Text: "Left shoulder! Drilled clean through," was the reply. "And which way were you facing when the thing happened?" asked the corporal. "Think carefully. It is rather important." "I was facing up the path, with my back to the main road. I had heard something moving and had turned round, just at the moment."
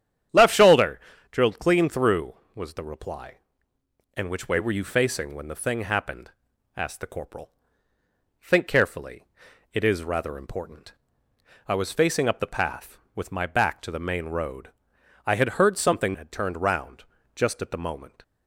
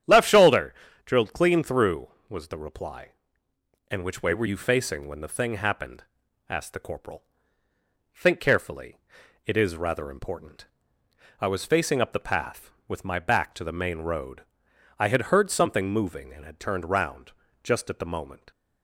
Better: second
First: starts louder than the rest; strong; until 1.6 s; 9.5 dB // skips "moving and"; at 16.1 s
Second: starts louder than the rest; strong; until 1.3 s; 9.5 dB

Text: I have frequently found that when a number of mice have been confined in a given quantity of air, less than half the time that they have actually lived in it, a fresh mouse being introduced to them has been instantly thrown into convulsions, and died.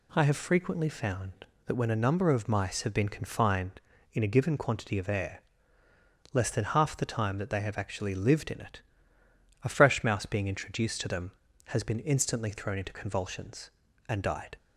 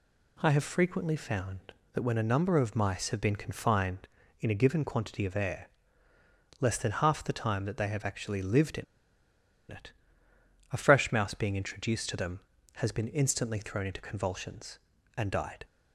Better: first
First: none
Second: pauses between "in" and "it"; noticeable; at 8.8 s; 0.86 s long

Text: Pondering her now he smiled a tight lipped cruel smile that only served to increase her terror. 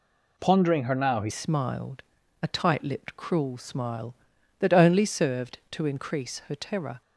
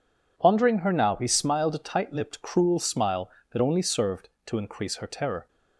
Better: second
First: changes voice at "smiled"; from 1.3 s on; 5.7 s long // pauses between "smiled" and "a"; at 2.0 s; 0.38 s long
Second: none

